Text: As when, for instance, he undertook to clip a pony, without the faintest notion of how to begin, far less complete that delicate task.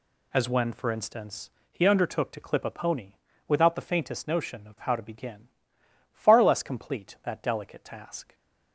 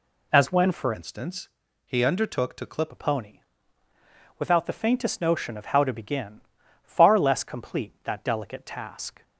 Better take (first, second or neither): first